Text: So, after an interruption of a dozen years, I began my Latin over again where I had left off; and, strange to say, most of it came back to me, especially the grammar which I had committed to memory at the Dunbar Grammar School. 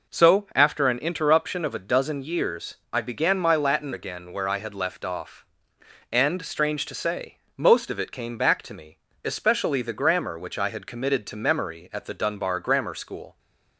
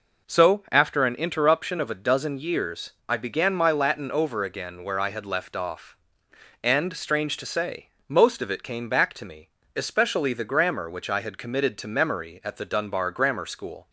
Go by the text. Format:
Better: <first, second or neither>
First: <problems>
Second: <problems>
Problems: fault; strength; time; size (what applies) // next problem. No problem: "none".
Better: second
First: skips "over"; at 3.9 s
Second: none